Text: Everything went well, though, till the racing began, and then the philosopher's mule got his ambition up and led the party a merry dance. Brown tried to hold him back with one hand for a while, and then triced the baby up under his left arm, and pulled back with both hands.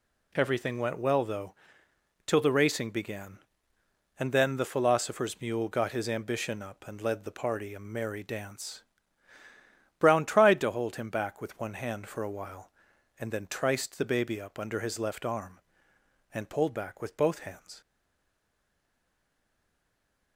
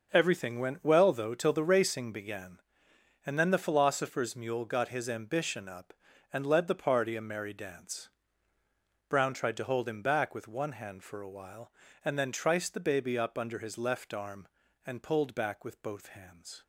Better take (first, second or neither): second